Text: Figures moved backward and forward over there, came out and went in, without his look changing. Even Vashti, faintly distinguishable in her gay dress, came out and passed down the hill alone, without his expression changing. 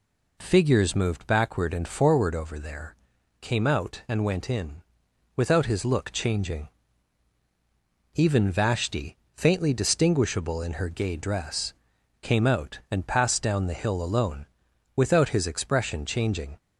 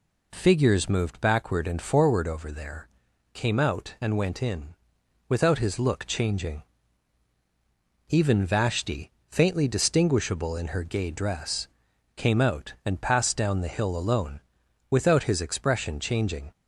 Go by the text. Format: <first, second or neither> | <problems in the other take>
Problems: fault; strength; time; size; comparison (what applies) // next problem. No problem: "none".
neither | none